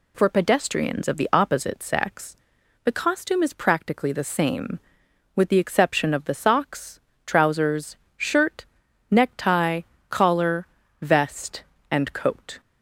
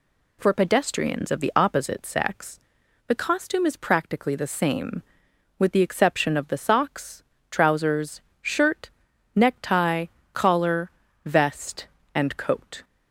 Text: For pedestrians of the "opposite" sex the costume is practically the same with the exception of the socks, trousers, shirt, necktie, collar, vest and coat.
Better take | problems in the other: neither | pauses between "sex" and "the"; noticeable; the same in both

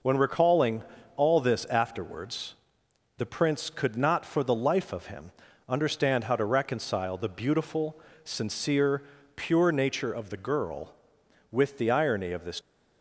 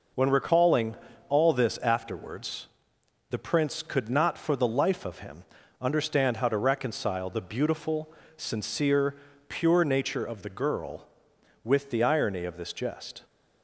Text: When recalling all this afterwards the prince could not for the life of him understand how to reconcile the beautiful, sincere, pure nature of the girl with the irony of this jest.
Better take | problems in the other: second | pauses between "recalling" and "all"; slight; at 0.8 s; 0.32 s long; slight in the second // pauses between "afterwards" and "the"; noticeable; at 2.5 s; 0.64 s long; noticeable in the second // pauses between "him" and "understand"; at 5.3 s; 0.38 s long; also in the second // stops before "jest"; at 12.6 s

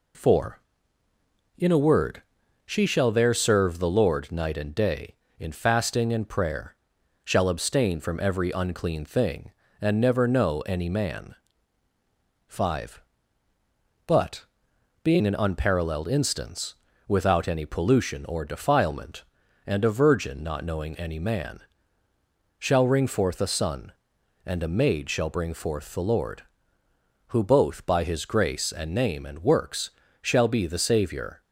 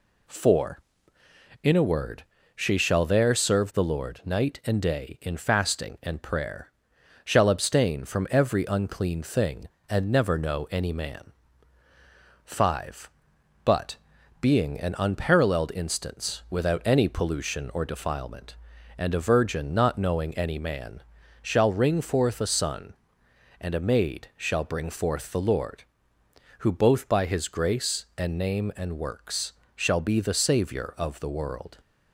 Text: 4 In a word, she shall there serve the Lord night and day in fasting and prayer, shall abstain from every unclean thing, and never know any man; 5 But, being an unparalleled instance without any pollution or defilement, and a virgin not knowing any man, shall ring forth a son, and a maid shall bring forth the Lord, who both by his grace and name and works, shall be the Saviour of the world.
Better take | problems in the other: second | pauses between "instance" and "without"; slight; at 16.7 s; 0.32 s long // stops before "of the world"; at 31.4 s

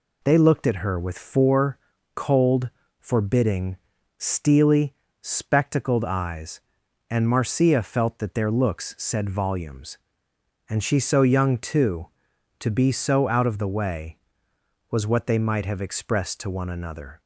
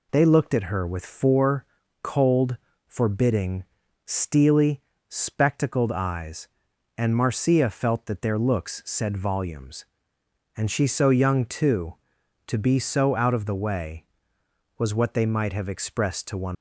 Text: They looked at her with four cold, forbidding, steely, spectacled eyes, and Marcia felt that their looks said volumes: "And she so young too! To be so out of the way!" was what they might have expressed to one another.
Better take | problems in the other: first | pauses between "four" and "cold"; slight; at 1.6 s; 0.36 s long; slight in the first // stops before "another"; at 16.5 s

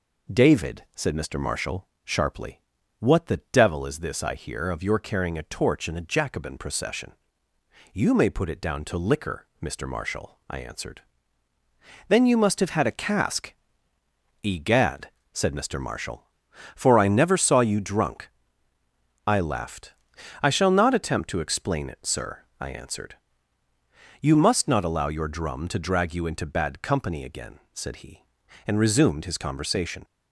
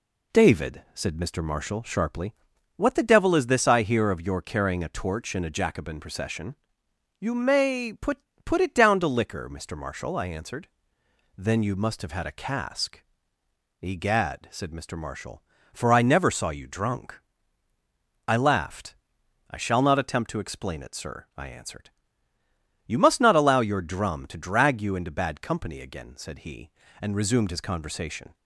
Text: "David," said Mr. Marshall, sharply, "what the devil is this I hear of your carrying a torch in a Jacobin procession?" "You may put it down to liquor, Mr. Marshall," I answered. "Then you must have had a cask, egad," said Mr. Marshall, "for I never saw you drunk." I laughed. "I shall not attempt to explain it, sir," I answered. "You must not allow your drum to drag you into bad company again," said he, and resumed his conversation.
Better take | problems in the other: first | says "put" twice; at 8.4 s

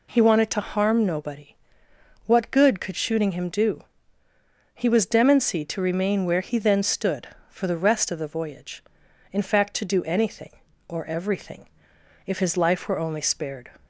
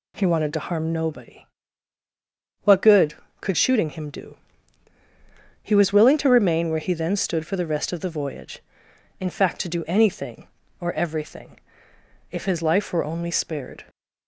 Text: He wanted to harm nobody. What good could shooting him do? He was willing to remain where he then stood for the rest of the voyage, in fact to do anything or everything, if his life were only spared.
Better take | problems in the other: second | says "demency" for "willing"; at 5.0 s

